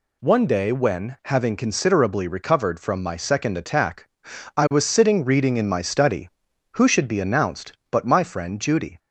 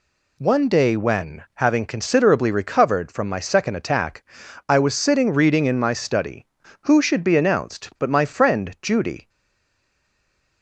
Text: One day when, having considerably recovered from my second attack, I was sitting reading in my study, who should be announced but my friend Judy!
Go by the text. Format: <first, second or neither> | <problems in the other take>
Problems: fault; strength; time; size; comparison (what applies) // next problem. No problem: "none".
first | stays silent after the last word; noticeable; from 9.2 s on; 1.4 s long